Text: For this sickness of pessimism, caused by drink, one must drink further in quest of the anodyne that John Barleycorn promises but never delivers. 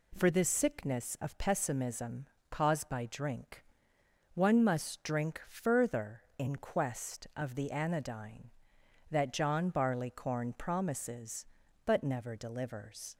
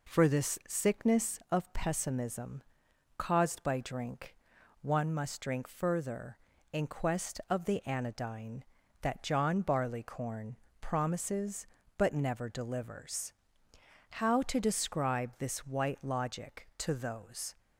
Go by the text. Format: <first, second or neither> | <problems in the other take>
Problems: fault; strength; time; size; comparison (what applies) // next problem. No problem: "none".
first | pauses between "Barleycorn" and "promises"; slight; at 10.5 s; 0.22 s long // goes on to say "How to describe this White Logic to those"; strong; from 14.1 s on; 3.4 s long